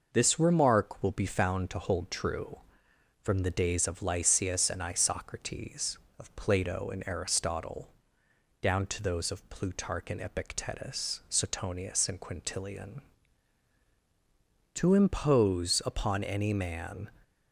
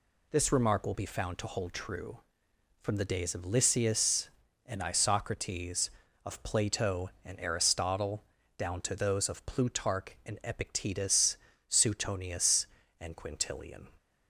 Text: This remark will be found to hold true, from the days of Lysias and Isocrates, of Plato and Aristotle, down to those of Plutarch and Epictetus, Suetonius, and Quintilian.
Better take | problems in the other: second | goes on to say "To impose upon any man"; strong; from 14.7 s on; 2.3 s long

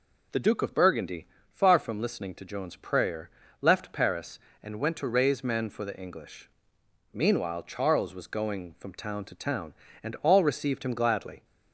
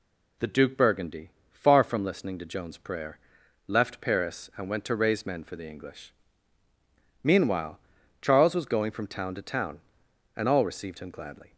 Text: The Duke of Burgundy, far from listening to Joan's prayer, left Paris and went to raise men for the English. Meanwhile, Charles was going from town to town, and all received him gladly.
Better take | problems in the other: first | skips "of"; at 0.7 s

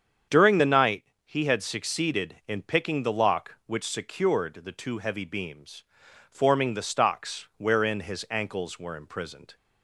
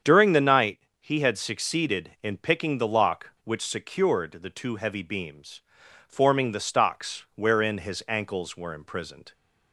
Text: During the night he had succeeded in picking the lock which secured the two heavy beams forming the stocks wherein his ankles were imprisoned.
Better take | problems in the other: neither | starts louder than the rest; strong; the same in both // pauses between "night" and "he"; slight; the same in both // pauses between "beams" and "forming"; noticeable; the same in both

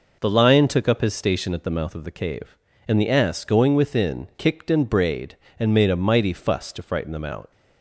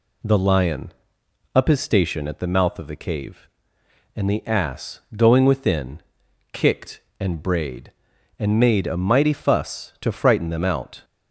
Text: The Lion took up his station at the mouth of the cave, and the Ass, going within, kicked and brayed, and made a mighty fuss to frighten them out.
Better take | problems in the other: first | skips "took"; at 1.2 s

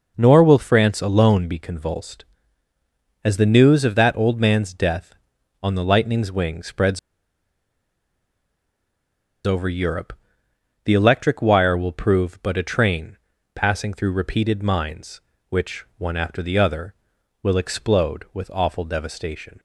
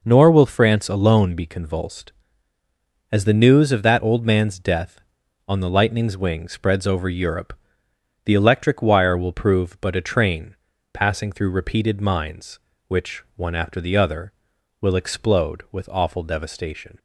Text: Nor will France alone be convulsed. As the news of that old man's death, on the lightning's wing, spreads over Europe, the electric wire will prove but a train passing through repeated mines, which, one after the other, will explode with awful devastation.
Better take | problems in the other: second | pauses between "spreads" and "over"; strong; at 6.9 s; 2.4 s long // pauses between "train" and "passing"; at 13.1 s; 0.38 s long; also in the second

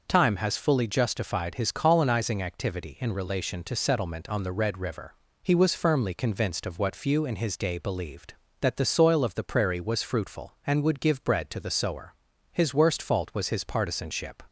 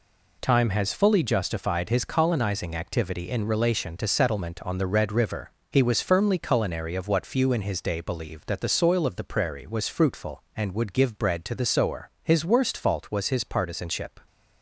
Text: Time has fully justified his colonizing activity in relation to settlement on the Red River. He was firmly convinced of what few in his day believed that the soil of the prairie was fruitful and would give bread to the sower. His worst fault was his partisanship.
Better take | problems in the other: first | says "culinary" for "convinced"; at 6.3 s

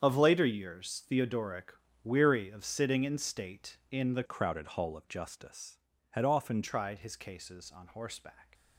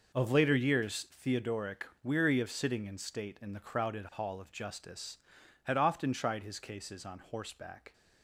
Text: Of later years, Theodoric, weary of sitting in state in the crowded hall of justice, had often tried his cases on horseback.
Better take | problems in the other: second | starts louder than the rest; strong; until 1.0 s; 8 dB // changes voice from "crowded" to "often"; from 4.2 to 6.6 s; 2.4 s long

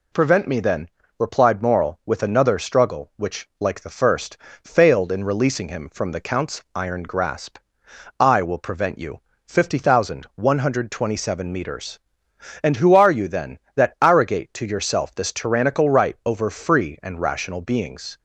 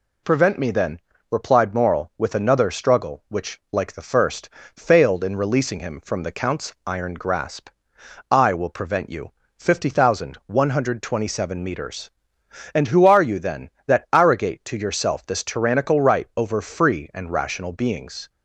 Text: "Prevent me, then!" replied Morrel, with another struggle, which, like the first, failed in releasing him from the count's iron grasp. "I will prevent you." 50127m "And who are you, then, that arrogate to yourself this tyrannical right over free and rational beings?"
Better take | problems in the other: neither | none

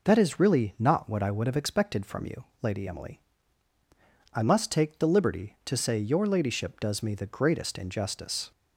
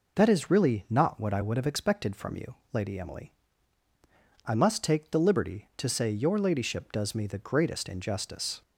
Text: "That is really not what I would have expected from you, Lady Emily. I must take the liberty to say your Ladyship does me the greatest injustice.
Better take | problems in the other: neither | none

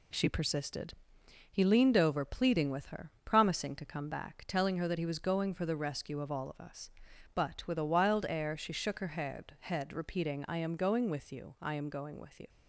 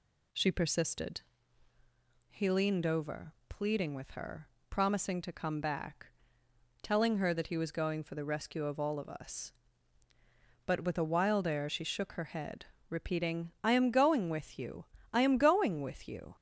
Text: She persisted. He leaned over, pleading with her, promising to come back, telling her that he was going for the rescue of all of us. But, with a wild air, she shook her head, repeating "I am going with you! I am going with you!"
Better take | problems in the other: second | says "head" twice; at 9.6 s

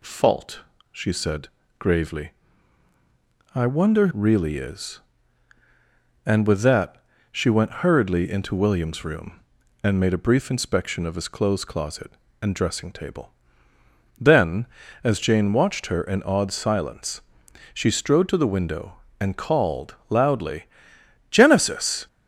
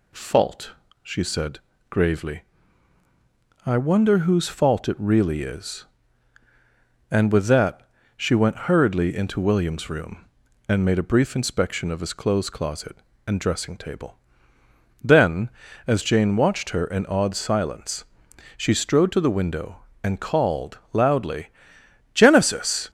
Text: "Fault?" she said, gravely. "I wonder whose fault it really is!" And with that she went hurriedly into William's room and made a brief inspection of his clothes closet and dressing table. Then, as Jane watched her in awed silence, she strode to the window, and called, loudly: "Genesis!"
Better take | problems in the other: second | skips "whose fault it"; at 4.1 s // pauses between "that" and "she"; slight; at 7.0 s; 0.26 s long; slight in the second

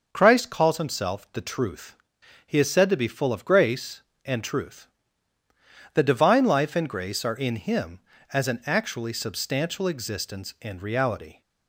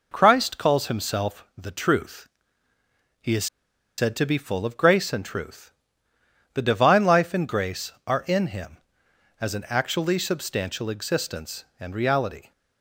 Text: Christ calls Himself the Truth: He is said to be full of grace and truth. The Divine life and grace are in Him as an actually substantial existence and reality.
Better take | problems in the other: first | pauses between "is" and "said"; noticeable; at 3.4 s; 0.51 s long

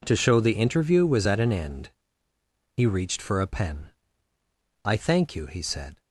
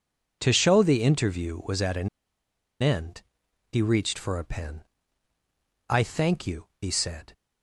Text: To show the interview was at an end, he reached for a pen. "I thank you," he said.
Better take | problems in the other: first | pauses between "an" and "end"; noticeable; at 2.0 s; 0.74 s long

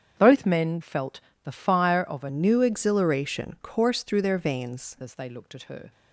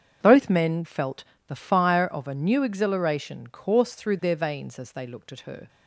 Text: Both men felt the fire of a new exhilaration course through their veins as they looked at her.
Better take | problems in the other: second | starts louder than the rest; strong; until 1.1 s; 8 dB; strong in the second // pauses between "felt" and "the"; slight; at 1.1 s; 0.24 s long; slight in the second // changes voice from "new" to "veins"; from 2.2 to 4.9 s; 2.7 s long

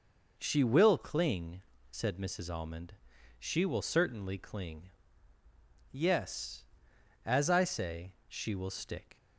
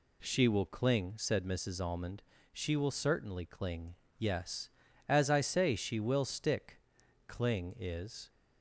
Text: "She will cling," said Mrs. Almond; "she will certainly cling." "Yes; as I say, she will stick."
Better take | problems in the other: first | goes on to say "Cling is"; noticeable; from 7.2 s on; 1.0 s long

